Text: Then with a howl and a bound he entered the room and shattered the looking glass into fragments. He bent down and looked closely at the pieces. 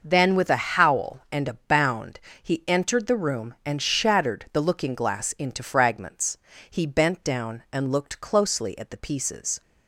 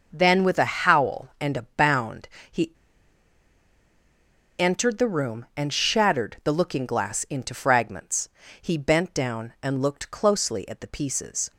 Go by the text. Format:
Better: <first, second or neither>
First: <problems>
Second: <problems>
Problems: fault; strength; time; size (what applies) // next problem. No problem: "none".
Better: first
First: pauses between "bound" and "he"; slight; at 2.1 s; 0.22 s long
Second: pauses between "bound" and "he"; slight; at 2.2 s; 0.22 s long // pauses between "he" and "entered"; strong; at 2.7 s; 1.8 s long